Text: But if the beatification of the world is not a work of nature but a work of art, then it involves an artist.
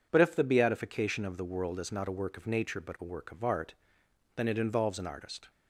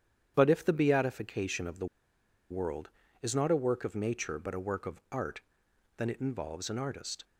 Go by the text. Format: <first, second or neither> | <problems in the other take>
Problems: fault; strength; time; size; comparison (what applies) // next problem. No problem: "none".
first | starts louder than the rest; strong; until 1.3 s; 9.5 dB // pauses between "the" and "world"; noticeable; at 1.8 s; 0.65 s long